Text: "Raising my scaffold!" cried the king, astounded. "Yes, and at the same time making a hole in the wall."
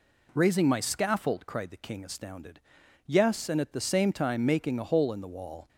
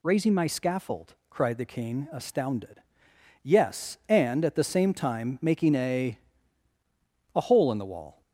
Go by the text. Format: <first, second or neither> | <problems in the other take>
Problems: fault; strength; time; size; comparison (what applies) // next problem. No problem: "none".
first | says "a" twice; at 7.3 s